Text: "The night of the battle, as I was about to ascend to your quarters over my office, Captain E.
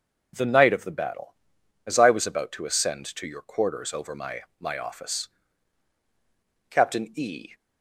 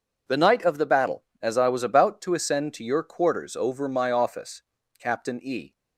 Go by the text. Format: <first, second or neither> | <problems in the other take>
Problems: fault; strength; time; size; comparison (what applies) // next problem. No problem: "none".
second | says "my" twice; at 4.5 s